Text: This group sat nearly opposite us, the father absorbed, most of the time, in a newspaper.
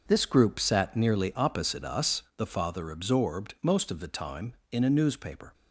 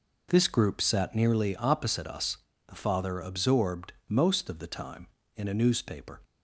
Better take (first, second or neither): second